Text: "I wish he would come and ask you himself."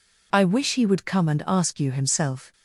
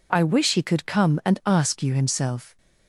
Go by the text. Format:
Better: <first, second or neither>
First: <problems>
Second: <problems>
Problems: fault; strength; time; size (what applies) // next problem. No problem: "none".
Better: first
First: none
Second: says "could" for "would"; at 0.6 s